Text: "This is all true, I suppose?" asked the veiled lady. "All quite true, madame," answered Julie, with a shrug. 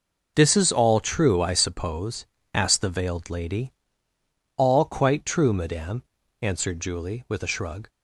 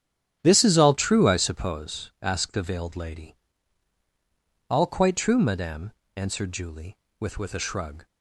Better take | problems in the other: first | starts louder than the rest; strong; until 1.4 s; 10 dB // says "with" twice; at 7.3 s

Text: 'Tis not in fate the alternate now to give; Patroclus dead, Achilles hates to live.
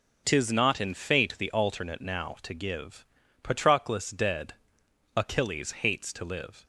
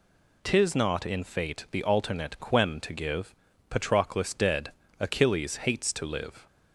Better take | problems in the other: first | says "quem" for "now"; at 2.3 s

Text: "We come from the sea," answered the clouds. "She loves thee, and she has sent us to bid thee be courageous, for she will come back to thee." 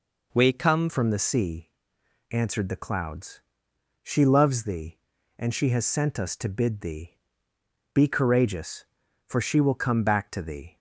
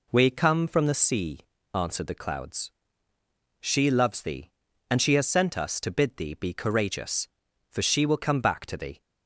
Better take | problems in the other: second | changes voice at "from"; from 0.8 s on; 9.9 s long // pauses between "thee" and "be"; noticeable; at 7.1 s; 0.76 s long

